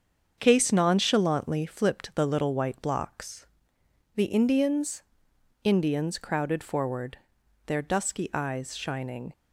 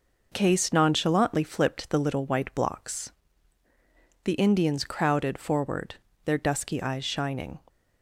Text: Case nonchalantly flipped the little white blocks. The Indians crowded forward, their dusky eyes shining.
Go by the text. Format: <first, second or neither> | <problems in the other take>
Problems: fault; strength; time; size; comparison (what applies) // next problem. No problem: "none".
second | starts louder than the rest; strong; until 1.4 s; 7 dB // says "Indians" twice; at 5.6 s